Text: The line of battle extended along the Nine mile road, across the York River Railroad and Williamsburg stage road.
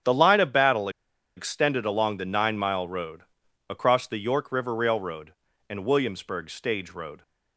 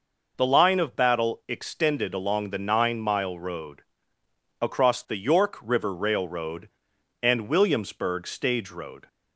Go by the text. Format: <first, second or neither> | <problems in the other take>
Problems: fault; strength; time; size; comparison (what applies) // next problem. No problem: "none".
second | starts louder than the rest; strong; until 1.5 s; 9.5 dB // pauses between "battle" and "extended"; noticeable; at 0.8 s; 0.47 s long